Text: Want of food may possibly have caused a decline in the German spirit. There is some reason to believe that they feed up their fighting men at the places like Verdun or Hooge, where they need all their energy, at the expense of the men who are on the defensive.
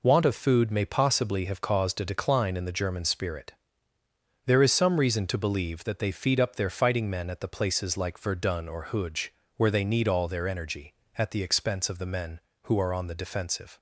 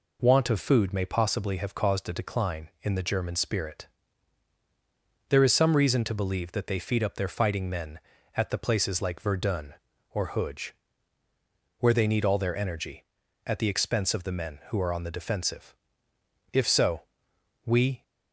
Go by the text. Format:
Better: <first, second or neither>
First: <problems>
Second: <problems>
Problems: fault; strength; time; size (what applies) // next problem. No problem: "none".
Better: first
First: none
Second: goes on to say "If so we"; from 16.5 s on; 1.5 s long